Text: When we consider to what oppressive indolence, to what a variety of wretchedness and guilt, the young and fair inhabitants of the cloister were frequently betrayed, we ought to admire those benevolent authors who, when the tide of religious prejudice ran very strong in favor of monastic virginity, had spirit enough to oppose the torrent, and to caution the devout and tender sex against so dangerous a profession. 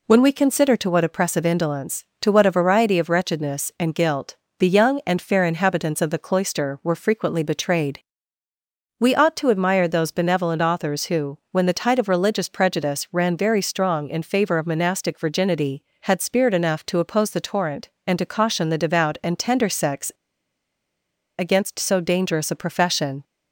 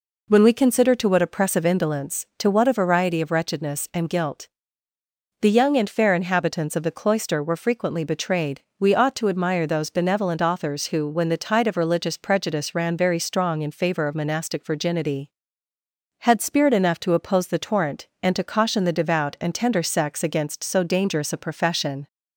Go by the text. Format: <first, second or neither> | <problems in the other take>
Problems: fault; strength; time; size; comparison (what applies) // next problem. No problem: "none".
second | pauses between "sex" and "against"; strong; at 20.1 s; 1.2 s long